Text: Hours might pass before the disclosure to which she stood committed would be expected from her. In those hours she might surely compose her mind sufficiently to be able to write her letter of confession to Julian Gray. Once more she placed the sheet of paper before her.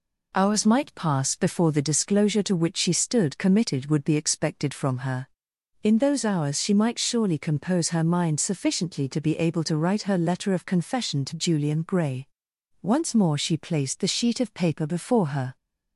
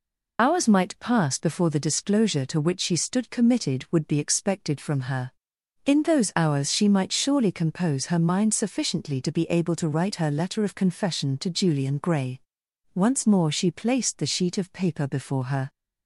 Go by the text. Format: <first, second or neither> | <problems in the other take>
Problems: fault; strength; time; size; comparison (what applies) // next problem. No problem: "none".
first | loses the start of "Hours"; at 0.3 s; 40 ms